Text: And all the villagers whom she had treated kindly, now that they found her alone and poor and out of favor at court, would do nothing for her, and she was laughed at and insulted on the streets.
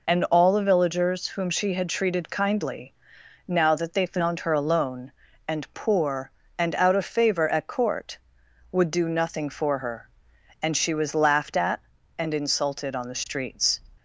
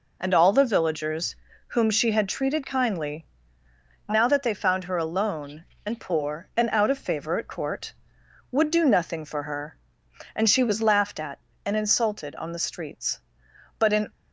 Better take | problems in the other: first | pauses between "villagers" and "whom"; slight; at 1.3 s; 0.32 s long // goes on to say "But in"; slight; from 13.7 s on; 0.32 s long

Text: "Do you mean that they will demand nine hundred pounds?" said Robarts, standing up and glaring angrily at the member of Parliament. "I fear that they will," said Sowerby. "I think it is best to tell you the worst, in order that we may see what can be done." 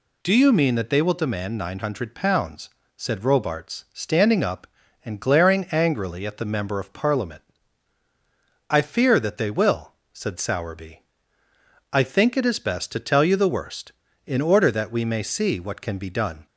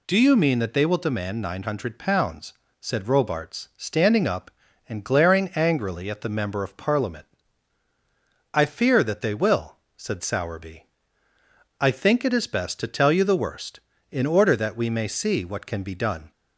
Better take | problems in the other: neither | none

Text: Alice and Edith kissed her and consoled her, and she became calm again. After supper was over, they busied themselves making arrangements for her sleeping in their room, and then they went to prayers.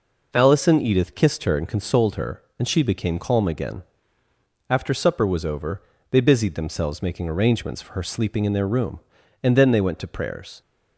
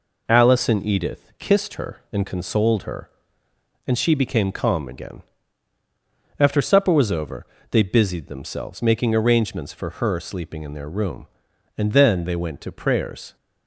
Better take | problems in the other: neither | none

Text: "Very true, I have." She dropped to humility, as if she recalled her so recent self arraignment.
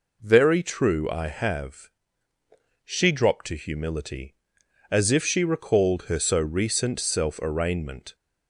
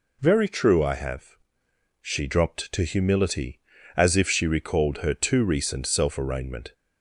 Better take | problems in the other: first | says "too" for "so"; at 5.1 s

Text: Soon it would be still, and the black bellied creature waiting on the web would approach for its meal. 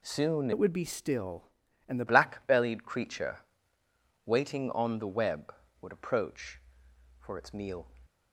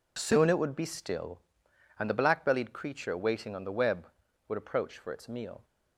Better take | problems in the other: second | changes voice from "it" to "the"; from 0.5 to 2.0 s; 1.5 s long // pauses between "creature" and "waiting"; noticeable; at 3.3 s; 0.88 s long

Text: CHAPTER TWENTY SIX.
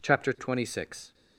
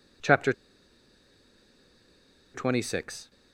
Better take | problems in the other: first | pauses between "CHAPTER" and "TWENTY"; strong; at 0.5 s; 2.0 s long

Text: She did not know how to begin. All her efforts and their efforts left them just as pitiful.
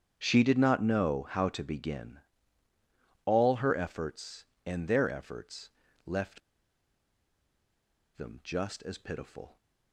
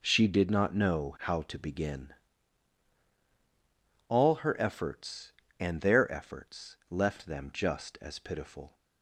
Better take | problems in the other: second | starts louder than the rest; strong; until 1.1 s; 8 dB // pauses between "efforts" and "left"; slight; at 5.6 s; 0.36 s long // pauses between "left" and "them"; strong; at 6.4 s; 1.7 s long

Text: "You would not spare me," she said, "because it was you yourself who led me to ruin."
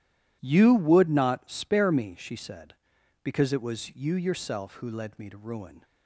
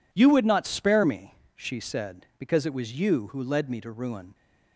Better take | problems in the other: first | skips "yourself"; at 3.2 s

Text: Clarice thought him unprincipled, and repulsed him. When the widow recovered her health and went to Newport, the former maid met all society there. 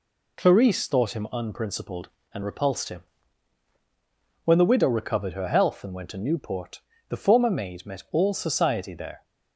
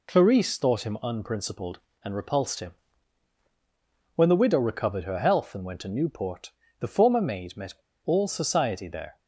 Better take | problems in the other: first | pauses between "met" and "all"; slight; at 7.7 s; 0.31 s long

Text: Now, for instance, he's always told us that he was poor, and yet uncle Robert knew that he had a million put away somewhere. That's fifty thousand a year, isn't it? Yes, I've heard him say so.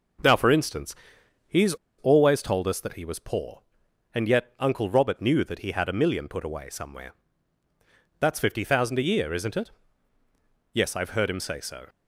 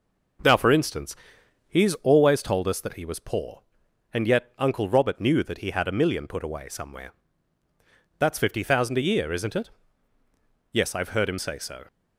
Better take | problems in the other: second | pauses between "he's" and "always"; slight; at 1.7 s; 0.24 s long

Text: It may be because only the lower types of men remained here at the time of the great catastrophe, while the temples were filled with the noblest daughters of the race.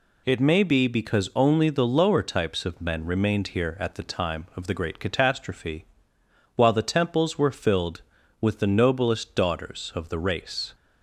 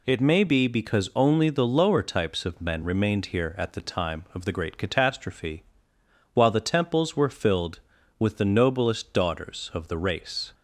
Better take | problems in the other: neither | none

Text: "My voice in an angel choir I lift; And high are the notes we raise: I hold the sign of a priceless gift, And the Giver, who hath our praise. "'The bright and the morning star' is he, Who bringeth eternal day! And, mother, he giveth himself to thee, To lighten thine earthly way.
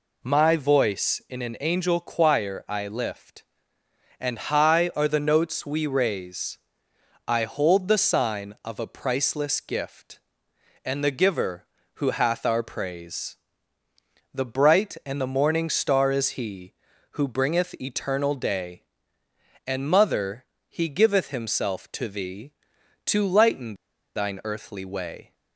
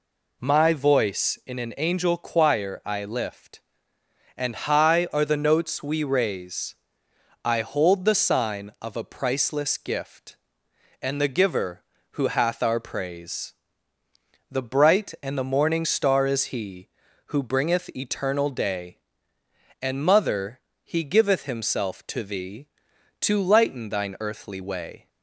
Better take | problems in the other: second | pauses between "lighten" and "thine"; at 23.7 s; 0.42 s long

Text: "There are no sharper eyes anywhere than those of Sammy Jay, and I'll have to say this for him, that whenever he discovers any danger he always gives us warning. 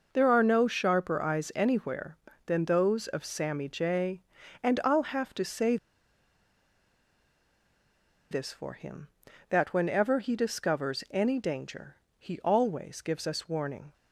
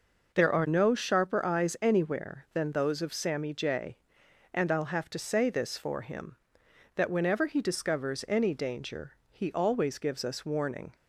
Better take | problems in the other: second | pauses between "say" and "this"; strong; at 5.7 s; 2.5 s long // pauses between "danger" and "he"; slight; at 11.9 s; 0.24 s long; slight in the second

